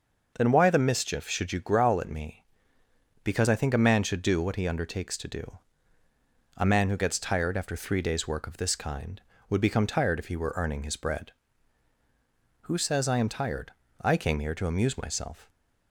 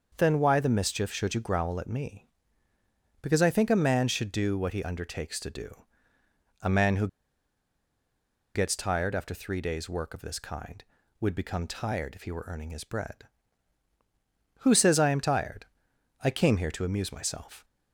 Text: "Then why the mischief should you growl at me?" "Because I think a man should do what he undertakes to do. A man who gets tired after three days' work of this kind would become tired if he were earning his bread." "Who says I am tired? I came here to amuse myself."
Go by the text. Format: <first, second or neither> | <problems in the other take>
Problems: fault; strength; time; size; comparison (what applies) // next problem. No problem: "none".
first | starts louder than the rest; until 1.1 s; 6.5 dB // pauses between "who" and "gets"; strong; at 7.0 s; 1.4 s long